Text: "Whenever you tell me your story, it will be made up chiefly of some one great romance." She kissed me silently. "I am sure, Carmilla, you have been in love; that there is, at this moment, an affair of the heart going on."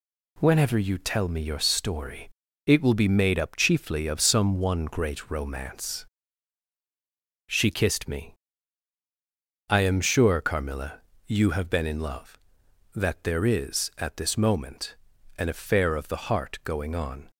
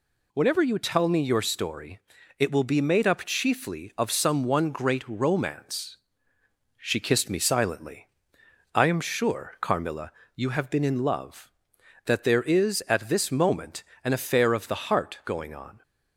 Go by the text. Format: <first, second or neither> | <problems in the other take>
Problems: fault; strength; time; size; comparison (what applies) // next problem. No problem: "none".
second | skips "silently"; at 9.0 s